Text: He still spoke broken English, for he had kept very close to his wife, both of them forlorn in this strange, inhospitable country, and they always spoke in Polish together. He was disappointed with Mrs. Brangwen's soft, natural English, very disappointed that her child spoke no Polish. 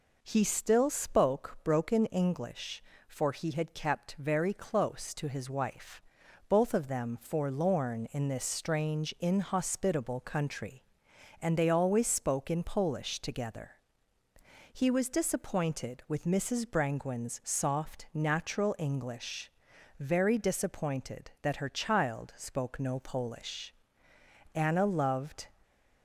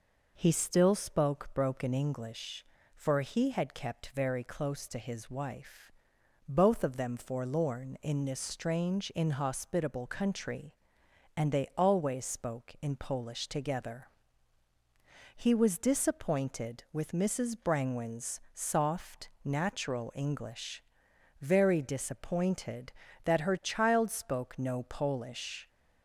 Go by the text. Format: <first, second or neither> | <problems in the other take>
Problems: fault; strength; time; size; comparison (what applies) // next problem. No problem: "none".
second | goes on to say "Anna loved"; noticeable; from 24.5 s on; 0.94 s long